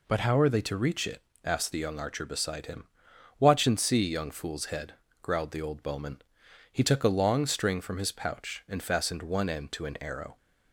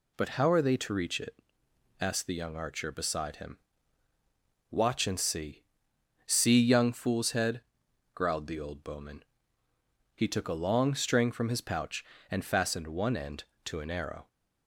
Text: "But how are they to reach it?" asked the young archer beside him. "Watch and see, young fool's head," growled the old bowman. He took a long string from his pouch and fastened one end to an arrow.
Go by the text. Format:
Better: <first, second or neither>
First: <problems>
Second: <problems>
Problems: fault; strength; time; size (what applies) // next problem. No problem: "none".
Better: first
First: none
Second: says "see" twice; at 6.2 s